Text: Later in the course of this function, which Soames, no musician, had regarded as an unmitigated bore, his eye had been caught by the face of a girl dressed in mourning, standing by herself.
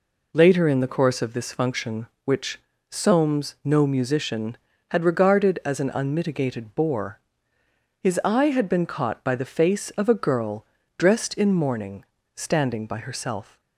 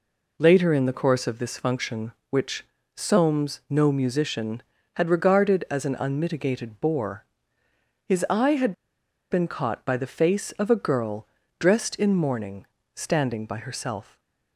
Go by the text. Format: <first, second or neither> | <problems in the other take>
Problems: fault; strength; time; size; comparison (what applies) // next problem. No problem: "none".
first | pauses between "which" and "Soames"; slight; at 2.6 s; 0.30 s long; slight in the first // pauses between "had" and "been"; noticeable; at 8.7 s; 0.58 s long // pauses between "girl" and "dressed"; slight; at 11.2 s; 0.32 s long; slight in the first // stays silent after the last word; slight; from 14.0 s on; 0.5 s long